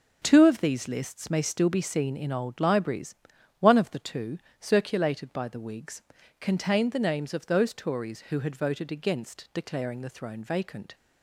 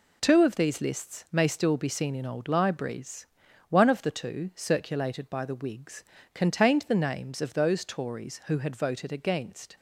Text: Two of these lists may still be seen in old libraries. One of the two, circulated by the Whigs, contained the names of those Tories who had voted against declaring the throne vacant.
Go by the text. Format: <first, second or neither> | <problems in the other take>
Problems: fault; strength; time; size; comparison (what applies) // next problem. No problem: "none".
first | stops before "declaring the throne vacant"; at 9.7 s